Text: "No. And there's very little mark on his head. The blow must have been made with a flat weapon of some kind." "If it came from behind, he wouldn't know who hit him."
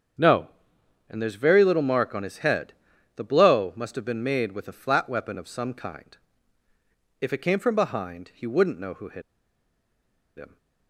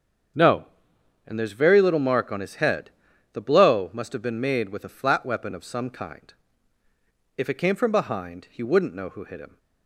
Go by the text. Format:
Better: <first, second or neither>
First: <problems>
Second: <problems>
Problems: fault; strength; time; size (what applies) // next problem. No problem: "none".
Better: second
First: starts louder than the rest; strong; until 1.8 s; 7.5 dB // pauses between "hit" and "him"; at 9.2 s; 1.1 s long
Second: starts louder than the rest; strong; until 1.9 s; 7.5 dB